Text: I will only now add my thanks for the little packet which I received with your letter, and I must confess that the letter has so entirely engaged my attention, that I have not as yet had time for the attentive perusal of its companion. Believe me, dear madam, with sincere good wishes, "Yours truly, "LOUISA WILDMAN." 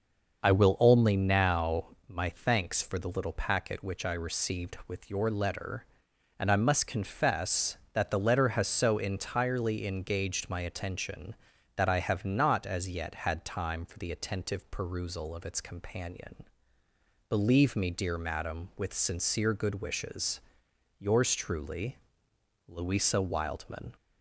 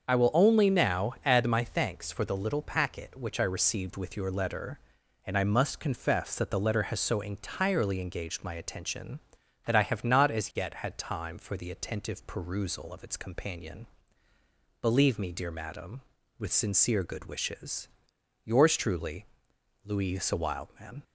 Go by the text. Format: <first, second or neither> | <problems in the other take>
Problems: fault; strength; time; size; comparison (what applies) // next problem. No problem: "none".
second | starts louder than the rest; noticeable; until 1.4 s; 6 dB; also in the second // skips "add"; at 1.9 s